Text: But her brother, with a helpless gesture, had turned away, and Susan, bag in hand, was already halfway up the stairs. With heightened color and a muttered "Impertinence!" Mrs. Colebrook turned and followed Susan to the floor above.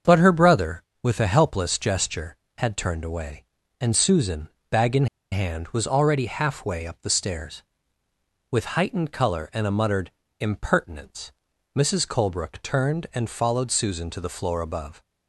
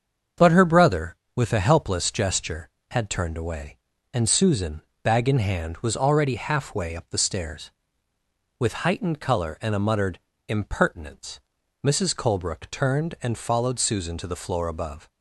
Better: second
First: starts louder than the rest; until 1.2 s; 7 dB // pauses between "in" and "hand"; slight; at 5.0 s; 0.25 s long // pauses between "muttered" and "Impertinence"; slight; at 10.1 s; 0.28 s long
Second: starts louder than the rest; until 1.5 s; 7 dB // pauses between "muttered" and "Impertinence"; slight; at 10.1 s; 0.28 s long

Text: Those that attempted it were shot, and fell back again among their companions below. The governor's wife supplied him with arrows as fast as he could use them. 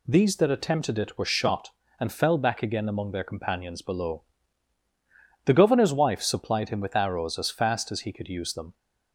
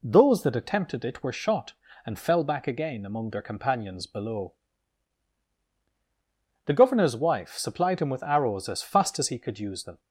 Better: second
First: says "These" for "Those"; at 0.0 s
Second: none

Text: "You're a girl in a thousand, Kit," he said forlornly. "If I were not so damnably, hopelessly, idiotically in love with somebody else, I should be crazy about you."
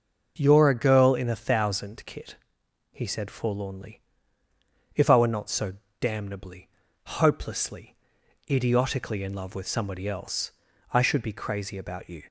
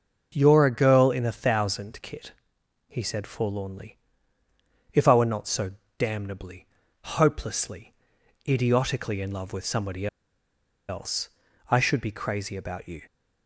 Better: first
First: pauses between "so" and "damnably"; slight; at 5.7 s; 0.26 s long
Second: pauses between "so" and "damnably"; slight; at 5.7 s; 0.26 s long // pauses between "somebody" and "else"; noticeable; at 10.0 s; 0.81 s long

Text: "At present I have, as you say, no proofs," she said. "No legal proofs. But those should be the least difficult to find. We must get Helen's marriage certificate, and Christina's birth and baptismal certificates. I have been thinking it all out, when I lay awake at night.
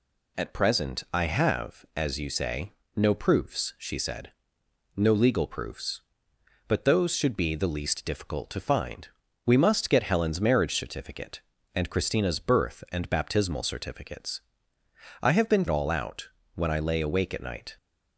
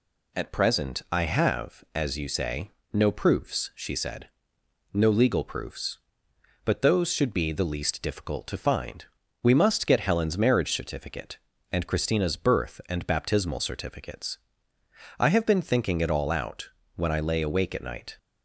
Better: second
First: skips "thinking it"; at 15.6 s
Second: none

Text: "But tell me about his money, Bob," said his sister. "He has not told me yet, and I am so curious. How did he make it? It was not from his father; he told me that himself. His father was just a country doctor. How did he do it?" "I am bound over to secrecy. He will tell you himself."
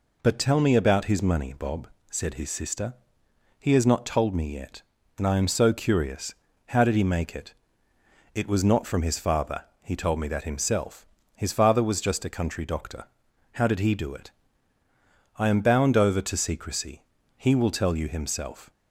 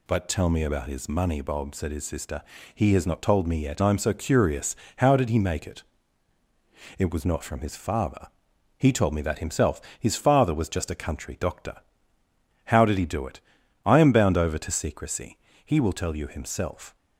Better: first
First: none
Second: skips "and"; at 3.8 s

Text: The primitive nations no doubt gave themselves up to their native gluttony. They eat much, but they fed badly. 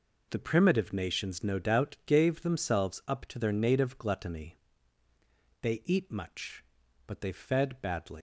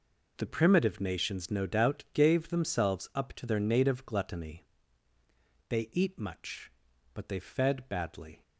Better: second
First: leaves "badly" unfinished; at 8.1 s; 135 ms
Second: none

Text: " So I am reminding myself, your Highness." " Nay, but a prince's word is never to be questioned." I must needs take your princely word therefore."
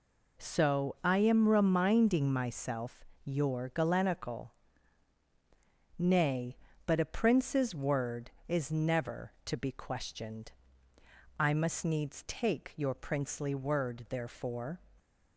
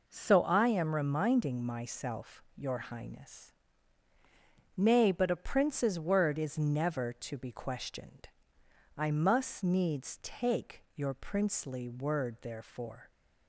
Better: second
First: says "Galenical" for "Highness"; at 3.6 s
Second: none

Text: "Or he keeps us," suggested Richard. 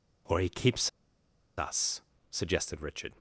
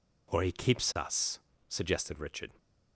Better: second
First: pauses between "keeps" and "us"; noticeable; at 0.8 s; 0.68 s long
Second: none

